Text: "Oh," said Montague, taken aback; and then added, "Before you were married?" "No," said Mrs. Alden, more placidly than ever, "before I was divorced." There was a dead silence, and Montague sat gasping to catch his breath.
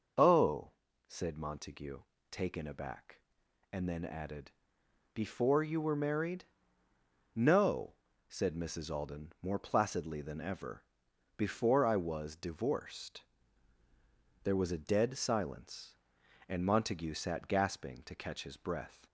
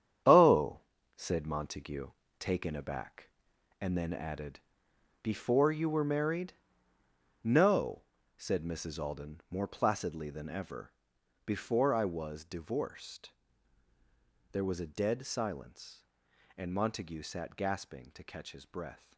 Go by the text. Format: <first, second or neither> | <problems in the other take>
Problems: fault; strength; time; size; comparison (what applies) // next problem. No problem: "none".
first | gets quieter; strong; throughout; 10.5 dB